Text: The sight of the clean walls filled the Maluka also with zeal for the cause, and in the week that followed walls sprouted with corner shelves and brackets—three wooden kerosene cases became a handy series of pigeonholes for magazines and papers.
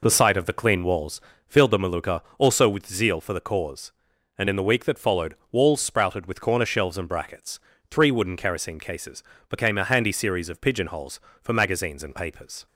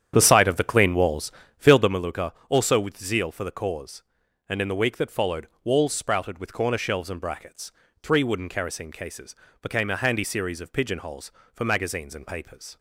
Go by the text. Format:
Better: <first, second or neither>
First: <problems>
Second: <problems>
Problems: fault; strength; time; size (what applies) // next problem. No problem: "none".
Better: first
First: pauses between "walls" and "filled"; slight; at 1.2 s; 0.26 s long // pauses between "Maluka" and "also"; slight; at 2.1 s; 0.18 s long // pauses between "followed" and "walls"; slight; at 5.3 s; 0.16 s long // pauses between "cases" and "became"; slight; at 9.2 s; 0.26 s long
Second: starts louder than the rest; strong; until 2.1 s; 9 dB // pauses between "walls" and "filled"; slight; at 1.3 s; 0.26 s long // pauses between "Maluka" and "also"; slight; at 2.3 s; 0.18 s long // pauses between "followed" and "walls"; slight; at 5.4 s; 0.16 s long // pauses between "cases" and "became"; slight; at 9.3 s; 0.26 s long